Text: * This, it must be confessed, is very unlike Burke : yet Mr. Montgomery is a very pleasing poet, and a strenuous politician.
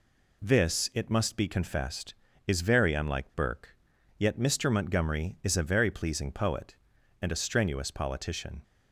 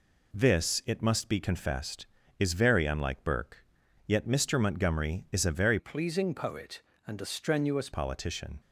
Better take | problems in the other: first | changes voice from "pleasing" to "strenuous"; from 5.7 to 7.8 s; 2.1 s long

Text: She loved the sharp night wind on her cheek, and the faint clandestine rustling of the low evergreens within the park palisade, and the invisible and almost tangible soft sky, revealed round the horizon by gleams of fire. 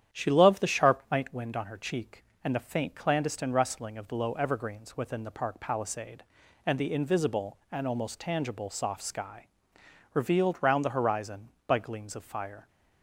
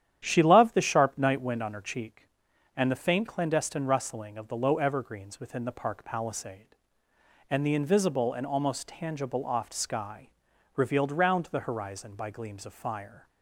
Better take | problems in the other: first | starts louder than the rest; strong; until 1.2 s; 10 dB; strong in the first // says "oft" for "soft"; at 9.4 s

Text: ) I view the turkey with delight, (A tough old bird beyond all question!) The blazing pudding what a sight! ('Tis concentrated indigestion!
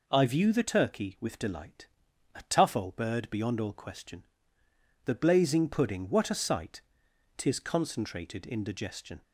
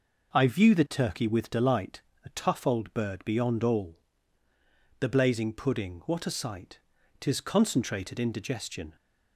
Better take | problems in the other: first | skips "question"; at 4.5 s

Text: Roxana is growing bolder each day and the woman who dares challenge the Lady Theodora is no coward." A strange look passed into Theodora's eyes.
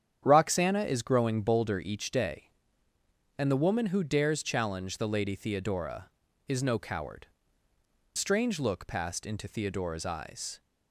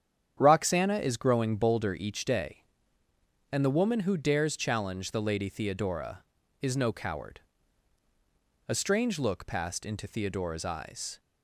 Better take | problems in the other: second | starts louder than the rest; strong; until 1.2 s; 8.5 dB; strong in the second // skips "A"; at 7.7 s

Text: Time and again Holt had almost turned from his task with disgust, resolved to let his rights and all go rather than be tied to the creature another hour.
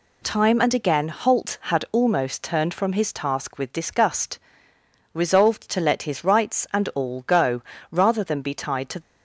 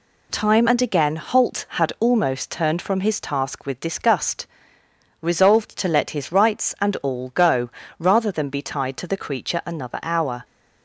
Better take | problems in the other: second | pauses between "go" and "rather"; slight; at 7.6 s; 0.28 s long; slight in the second // stops before "the creature another hour"; at 9.0 s

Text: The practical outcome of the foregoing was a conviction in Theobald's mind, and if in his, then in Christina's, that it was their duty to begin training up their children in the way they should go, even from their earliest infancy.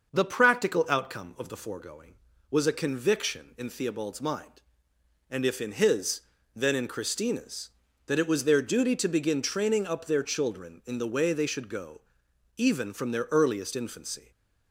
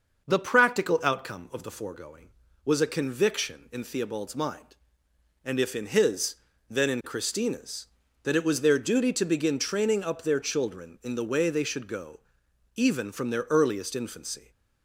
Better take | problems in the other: neither | starts louder than the rest; the same in both

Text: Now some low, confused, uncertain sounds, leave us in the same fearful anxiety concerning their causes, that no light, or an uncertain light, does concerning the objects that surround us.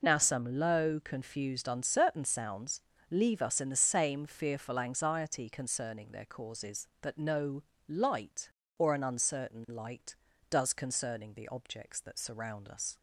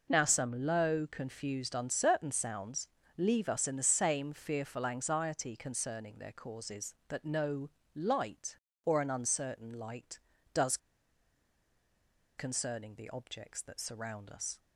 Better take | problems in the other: first | pauses between "no" and "light"; slight; at 7.6 s; 0.26 s long; slight in the first // pauses between "does" and "concerning"; strong; at 10.7 s; 1.6 s long

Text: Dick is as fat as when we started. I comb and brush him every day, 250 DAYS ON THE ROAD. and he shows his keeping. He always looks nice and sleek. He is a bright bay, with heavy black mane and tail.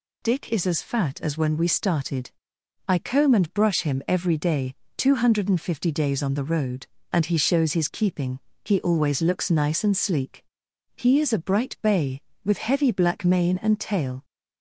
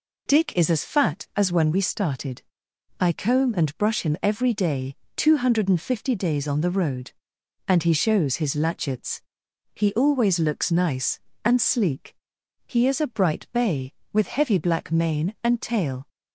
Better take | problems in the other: first | says "latchets" for "keeping"; at 8.5 s

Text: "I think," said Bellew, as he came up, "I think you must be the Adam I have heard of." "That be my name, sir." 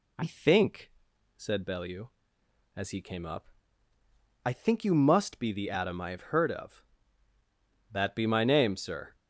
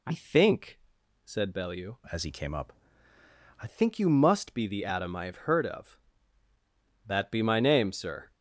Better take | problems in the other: first | changes voice from "as" to "I"; from 2.1 to 3.6 s; 1.5 s long

